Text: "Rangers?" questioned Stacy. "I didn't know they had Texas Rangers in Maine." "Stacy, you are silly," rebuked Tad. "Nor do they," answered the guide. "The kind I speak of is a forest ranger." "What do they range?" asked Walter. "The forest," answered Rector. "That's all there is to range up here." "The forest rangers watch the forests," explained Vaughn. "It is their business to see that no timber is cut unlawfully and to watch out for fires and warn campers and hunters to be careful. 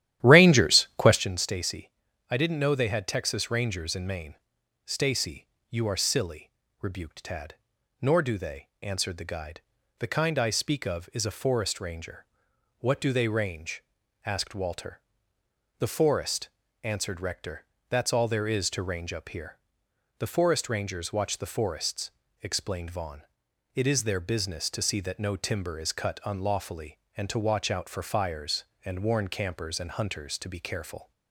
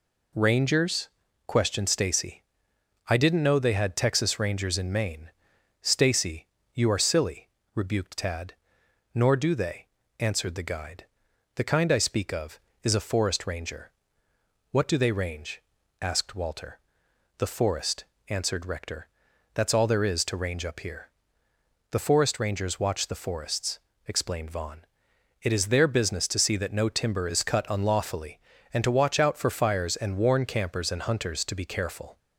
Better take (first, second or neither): second